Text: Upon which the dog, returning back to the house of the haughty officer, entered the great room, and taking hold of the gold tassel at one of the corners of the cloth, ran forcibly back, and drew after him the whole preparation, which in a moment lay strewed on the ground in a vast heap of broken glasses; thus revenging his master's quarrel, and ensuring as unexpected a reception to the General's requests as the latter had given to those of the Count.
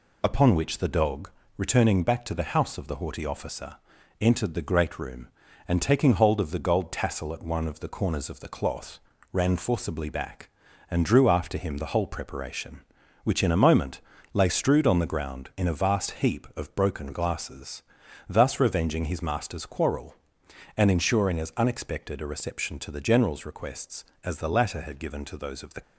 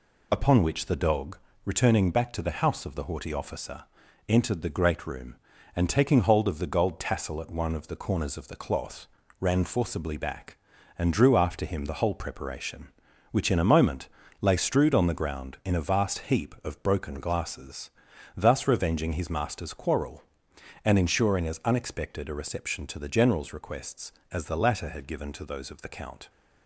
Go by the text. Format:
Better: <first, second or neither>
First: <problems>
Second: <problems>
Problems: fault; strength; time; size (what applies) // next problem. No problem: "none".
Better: second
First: pauses between "moment" and "lay"; slight; at 13.9 s; 0.32 s long // stops before "Count"; at 25.8 s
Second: pauses between "moment" and "lay"; slight; at 14.0 s; 0.32 s long